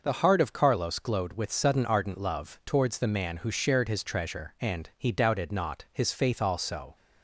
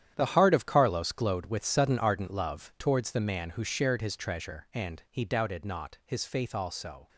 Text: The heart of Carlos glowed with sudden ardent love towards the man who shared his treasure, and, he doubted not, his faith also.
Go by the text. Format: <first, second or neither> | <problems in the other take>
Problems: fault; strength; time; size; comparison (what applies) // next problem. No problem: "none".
first | gets quieter; strong; throughout; 12 dB